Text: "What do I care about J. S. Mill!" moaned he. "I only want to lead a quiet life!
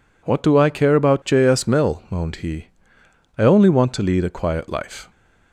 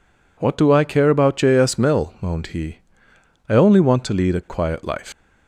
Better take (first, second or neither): first